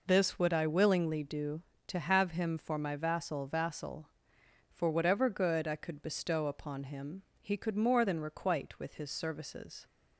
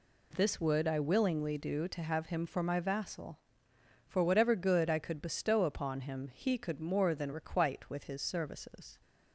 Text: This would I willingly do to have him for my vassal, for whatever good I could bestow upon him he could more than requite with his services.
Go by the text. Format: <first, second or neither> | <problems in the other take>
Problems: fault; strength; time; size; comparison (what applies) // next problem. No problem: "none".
second | says "vassal" twice; at 3.4 s // pauses between "him" and "he"; slight; at 7.2 s; 0.18 s long